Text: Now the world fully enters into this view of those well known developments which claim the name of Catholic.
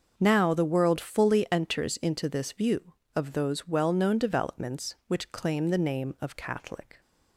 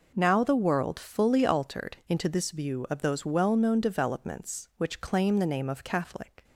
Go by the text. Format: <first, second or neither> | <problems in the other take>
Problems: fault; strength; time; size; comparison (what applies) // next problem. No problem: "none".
first | says "altered" for "enters"; at 1.4 s